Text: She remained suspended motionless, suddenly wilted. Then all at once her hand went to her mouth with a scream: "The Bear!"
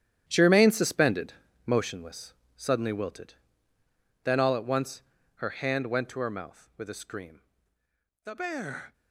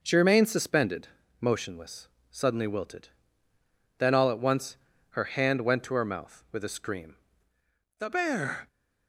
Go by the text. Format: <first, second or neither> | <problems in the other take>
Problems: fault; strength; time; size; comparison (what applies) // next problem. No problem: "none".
second | gets quieter; strong; throughout; 12 dB // pauses between "suspended" and "motionless"; slight; at 1.3 s; 0.36 s long; slight in the second // pauses between "once" and "her"; slight; at 5.0 s; 0.34 s long; slight in the second